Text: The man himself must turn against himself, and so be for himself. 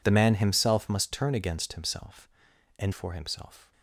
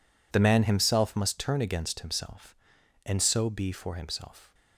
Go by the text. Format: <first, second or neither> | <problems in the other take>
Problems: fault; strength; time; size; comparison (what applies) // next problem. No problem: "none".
second | skips "so be"; at 2.9 s